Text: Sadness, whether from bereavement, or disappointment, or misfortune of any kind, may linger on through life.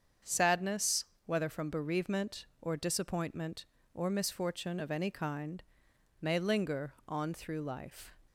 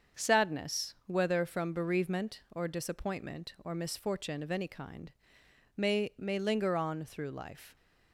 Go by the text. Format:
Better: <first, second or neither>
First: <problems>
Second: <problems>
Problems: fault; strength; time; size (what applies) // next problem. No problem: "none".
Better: first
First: starts louder than the rest; strong; until 1.4 s; 7.5 dB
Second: starts louder than the rest; until 1.3 s; 7 dB // says "may" twice; at 6.1 s